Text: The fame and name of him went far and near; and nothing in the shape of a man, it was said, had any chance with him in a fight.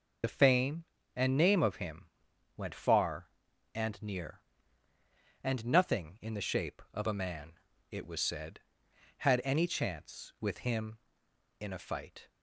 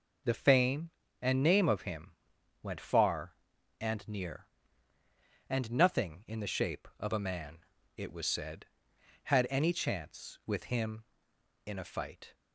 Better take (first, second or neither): second